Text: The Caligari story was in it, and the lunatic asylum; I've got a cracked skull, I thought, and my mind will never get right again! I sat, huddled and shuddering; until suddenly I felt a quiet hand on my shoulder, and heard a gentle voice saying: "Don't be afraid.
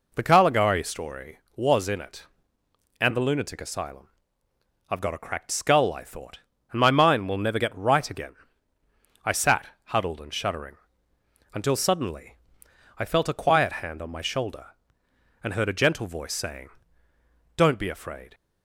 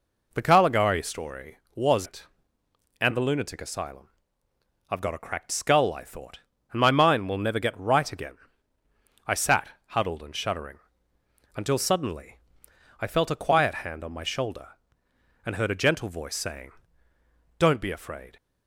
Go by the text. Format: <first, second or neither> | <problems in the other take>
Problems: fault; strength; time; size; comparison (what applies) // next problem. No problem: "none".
first | skips "in"; at 2.0 s // pauses between "suddenly" and "I"; noticeable; at 12.3 s; 0.64 s long; noticeable in the first